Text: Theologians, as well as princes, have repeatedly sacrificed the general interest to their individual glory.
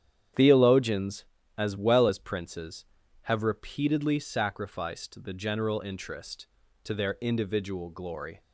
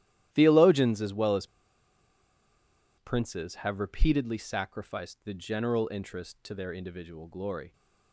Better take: first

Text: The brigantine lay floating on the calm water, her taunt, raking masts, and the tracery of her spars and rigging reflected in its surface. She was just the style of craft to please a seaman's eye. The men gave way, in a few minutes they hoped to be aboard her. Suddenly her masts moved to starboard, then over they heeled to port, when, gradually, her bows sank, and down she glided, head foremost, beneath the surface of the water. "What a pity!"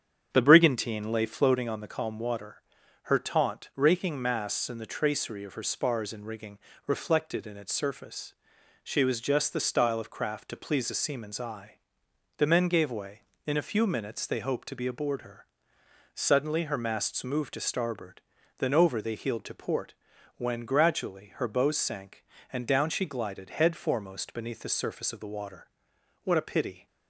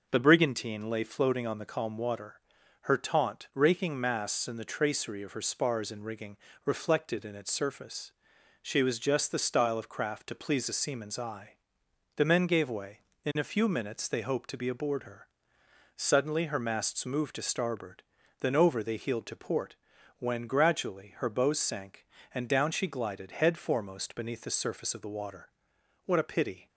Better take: second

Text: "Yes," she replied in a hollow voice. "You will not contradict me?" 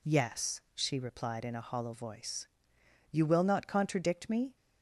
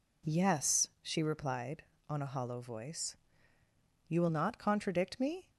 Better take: first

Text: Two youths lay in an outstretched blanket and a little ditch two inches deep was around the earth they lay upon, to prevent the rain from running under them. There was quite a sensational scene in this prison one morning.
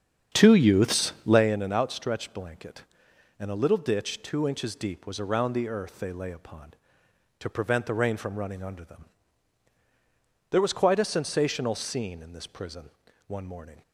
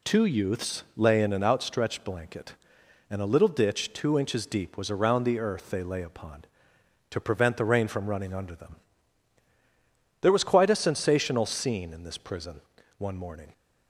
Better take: second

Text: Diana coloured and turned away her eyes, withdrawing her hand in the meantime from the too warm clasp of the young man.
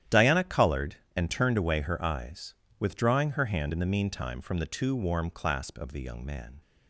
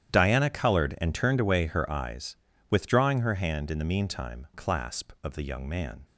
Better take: first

